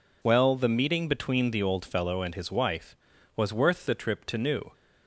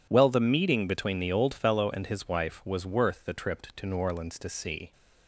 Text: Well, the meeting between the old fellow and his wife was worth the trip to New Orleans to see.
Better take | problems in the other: second | stops before "Orleans to see"; at 4.7 s

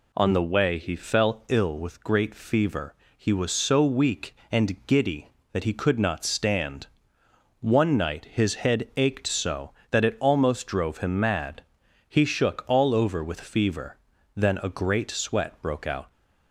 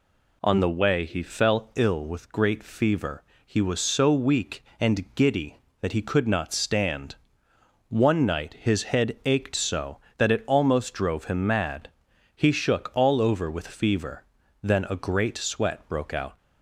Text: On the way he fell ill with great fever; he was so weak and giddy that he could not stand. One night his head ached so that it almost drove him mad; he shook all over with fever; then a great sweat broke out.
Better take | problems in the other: neither | none

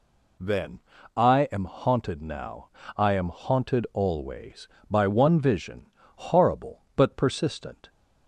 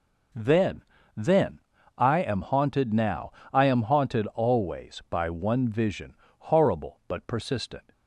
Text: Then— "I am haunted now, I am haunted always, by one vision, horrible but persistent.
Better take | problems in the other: first | says "Then" twice; at 1.1 s

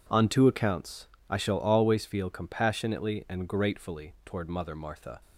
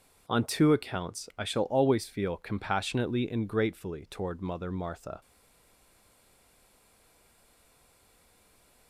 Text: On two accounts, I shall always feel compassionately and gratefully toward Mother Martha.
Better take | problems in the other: first | stays silent after the last word; strong; from 5.2 s on; 3.6 s long

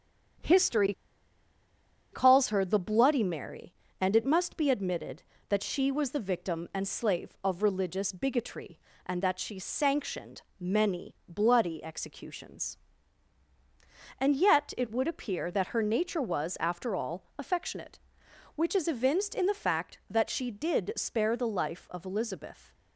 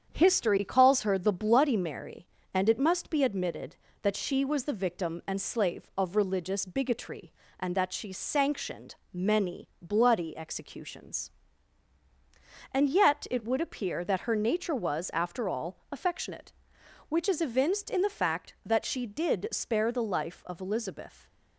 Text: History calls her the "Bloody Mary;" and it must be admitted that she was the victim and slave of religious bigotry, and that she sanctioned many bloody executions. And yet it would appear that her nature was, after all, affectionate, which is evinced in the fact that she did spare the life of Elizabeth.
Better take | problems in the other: second | starts louder than the rest; strong; until 2.6 s; 8 dB; strong in the second // pauses between "History" and "calls"; at 0.9 s; 1.2 s long // pauses between "sanctioned" and "many"; slight; at 10.4 s; 0.18 s long; slight in the second

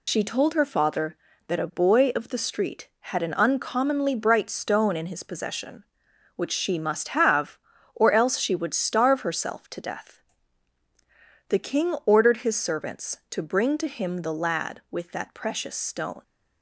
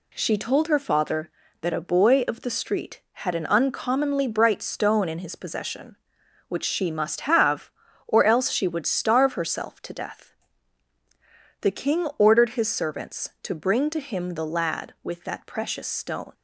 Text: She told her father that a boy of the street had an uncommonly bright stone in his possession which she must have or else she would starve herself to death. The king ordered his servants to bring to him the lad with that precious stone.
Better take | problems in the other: second | loses the start of "She"; at 0.0 s; 95 ms

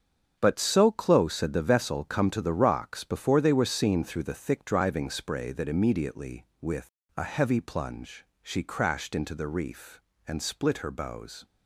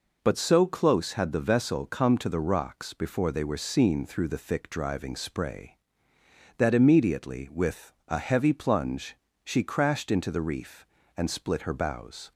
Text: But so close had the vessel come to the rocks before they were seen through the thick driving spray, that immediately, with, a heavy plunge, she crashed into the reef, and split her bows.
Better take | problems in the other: second | gets quieter; strong; throughout; 9 dB

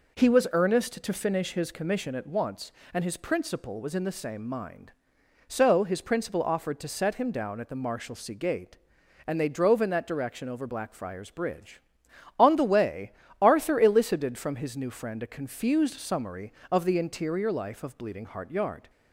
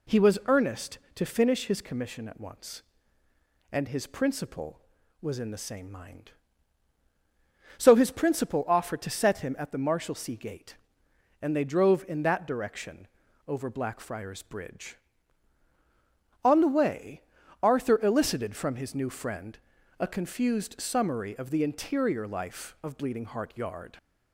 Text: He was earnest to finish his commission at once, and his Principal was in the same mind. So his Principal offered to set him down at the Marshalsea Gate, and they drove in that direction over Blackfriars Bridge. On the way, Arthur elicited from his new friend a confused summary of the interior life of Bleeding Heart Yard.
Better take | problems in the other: first | skips "down"; at 9.5 s // pauses between "direction" and "over"; at 13.0 s; 0.40 s long // pauses between "friend" and "a"; at 19.5 s; 0.42 s long

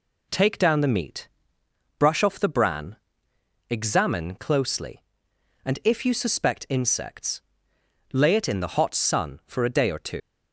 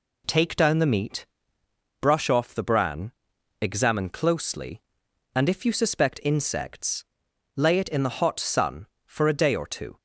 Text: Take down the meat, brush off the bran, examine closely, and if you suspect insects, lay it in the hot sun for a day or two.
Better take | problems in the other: second | leaves "two" unfinished; at 10.2 s; 125 ms

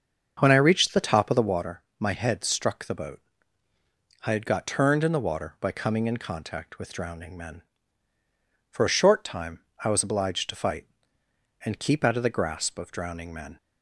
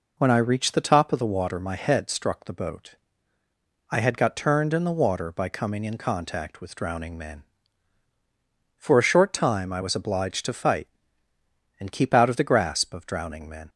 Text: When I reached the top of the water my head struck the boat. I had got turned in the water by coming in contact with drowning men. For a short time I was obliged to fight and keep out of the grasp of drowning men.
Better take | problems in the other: second | starts louder than the rest; until 1.7 s; 7 dB // pauses between "water" and "my"; slight; at 1.8 s; 0.15 s long // pauses between "time" and "I"; slight; at 9.6 s; 0.22 s long

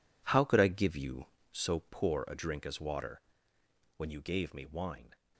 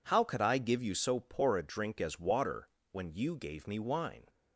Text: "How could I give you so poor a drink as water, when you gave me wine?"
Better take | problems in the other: second | gets quieter; strong; throughout; 13 dB

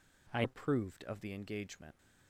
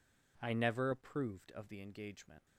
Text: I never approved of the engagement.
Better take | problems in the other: second | skips "never"; at 0.4 s

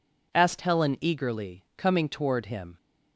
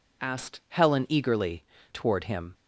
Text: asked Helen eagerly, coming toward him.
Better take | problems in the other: first | skips "coming"; at 1.7 s

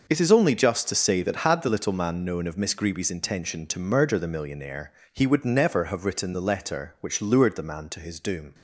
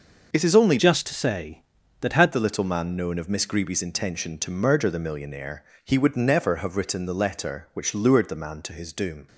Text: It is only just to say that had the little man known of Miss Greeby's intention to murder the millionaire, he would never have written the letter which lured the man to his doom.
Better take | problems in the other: first | changes voice from "just" to "had"; from 0.7 to 2.3 s; 1.6 s long

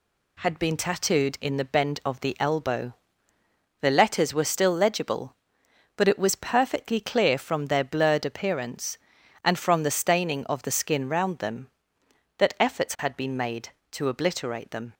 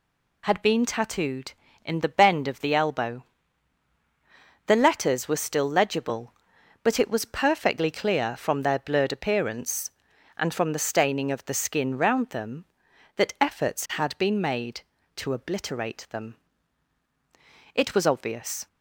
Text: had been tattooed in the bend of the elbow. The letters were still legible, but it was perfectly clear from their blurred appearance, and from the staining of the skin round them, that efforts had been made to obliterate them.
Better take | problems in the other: first | goes on to say "It was obvious"; noticeable; from 17.7 s on; 0.92 s long

